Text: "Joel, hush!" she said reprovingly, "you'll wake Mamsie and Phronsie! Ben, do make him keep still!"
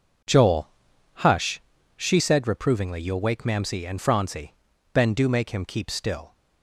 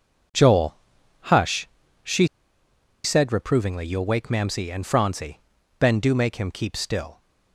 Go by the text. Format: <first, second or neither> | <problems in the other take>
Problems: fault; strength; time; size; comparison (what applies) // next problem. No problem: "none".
first | pauses between "she" and "said"; noticeable; at 2.2 s; 0.76 s long